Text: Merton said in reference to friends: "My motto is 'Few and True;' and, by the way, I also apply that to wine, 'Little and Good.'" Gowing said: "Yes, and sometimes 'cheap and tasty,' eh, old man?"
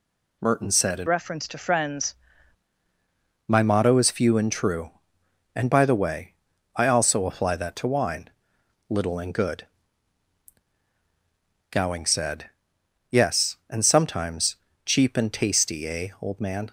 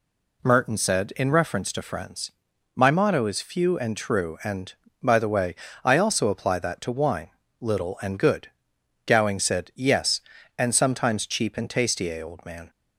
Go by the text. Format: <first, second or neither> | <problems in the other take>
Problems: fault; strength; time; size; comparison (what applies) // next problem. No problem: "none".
second | changes voice from "reference" to "friends"; from 1.0 to 2.1 s; 1.1 s long // pauses between "sometimes" and "cheap"; slight; at 14.5 s; 0.30 s long